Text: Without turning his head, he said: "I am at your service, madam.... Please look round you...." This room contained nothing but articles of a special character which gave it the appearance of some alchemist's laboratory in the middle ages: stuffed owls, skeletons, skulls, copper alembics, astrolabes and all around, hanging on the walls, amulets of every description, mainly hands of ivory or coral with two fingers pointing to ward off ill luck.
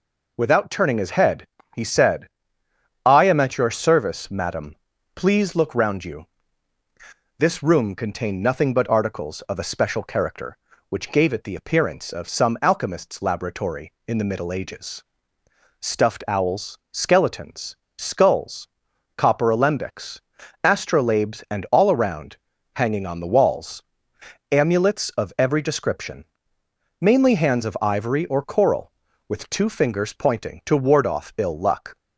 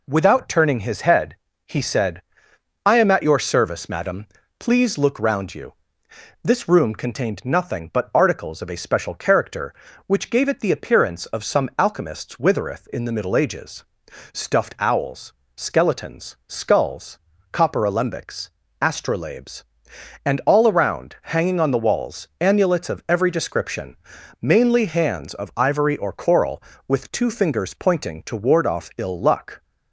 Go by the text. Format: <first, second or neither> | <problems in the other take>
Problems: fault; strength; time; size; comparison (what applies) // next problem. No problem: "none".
first | says "withereth" for "laboratory"; at 12.3 s